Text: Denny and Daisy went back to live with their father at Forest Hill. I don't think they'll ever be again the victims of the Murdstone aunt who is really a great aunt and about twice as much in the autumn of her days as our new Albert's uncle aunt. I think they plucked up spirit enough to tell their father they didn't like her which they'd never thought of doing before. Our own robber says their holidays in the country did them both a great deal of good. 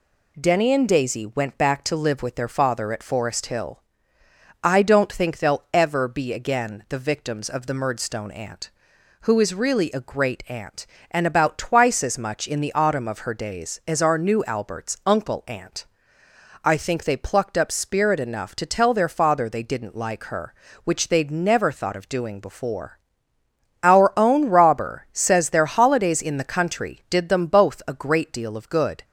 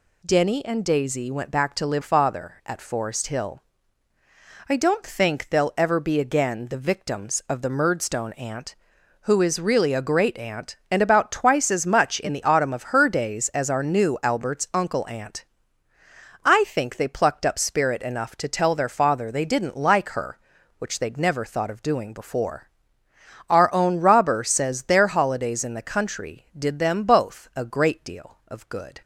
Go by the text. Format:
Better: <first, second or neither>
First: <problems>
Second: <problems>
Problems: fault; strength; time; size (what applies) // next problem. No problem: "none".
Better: first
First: none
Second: skips "with their"; at 2.0 s